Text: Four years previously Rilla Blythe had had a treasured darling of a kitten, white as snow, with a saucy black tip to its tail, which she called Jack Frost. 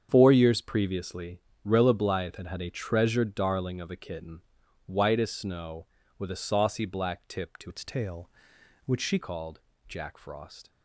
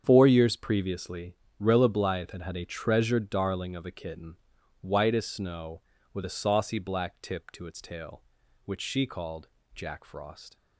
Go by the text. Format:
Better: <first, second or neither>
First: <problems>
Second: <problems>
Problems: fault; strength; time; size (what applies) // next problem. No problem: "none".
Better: second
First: starts louder than the rest; strong; until 1.1 s; 7.5 dB // pauses between "previously" and "Rilla"; slight; at 1.3 s; 0.26 s long // changes voice from "its" to "she"; from 7.6 to 9.1 s; 1.5 s long // pauses between "called" and "Jack"; slight; at 9.5 s; 0.30 s long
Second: starts louder than the rest; strong; until 1.0 s; 7.5 dB // pauses between "previously" and "Rilla"; slight; at 1.3 s; 0.26 s long // pauses between "called" and "Jack"; slight; at 9.4 s; 0.29 s long